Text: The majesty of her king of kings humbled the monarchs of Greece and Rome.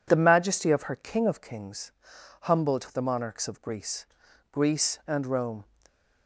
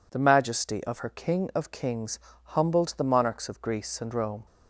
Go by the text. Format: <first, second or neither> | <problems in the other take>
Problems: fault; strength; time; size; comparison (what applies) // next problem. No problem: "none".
second | pauses between "kings" and "humbled"; noticeable; at 1.9 s; 0.50 s long; slight in the second // says "Greece" twice; at 4.5 s